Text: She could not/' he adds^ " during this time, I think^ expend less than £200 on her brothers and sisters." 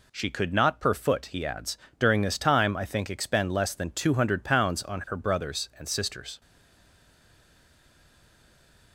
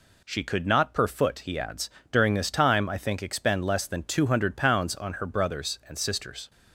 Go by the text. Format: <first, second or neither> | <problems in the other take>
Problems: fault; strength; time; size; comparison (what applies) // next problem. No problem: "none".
second | stays silent after the last word; strong; from 6.4 s on; 2.5 s long